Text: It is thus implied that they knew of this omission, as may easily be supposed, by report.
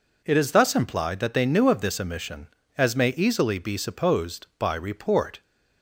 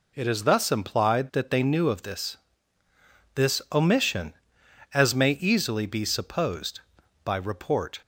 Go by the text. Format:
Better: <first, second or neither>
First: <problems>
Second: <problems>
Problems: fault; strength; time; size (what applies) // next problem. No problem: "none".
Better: first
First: none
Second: says "this" twice; at 3.3 s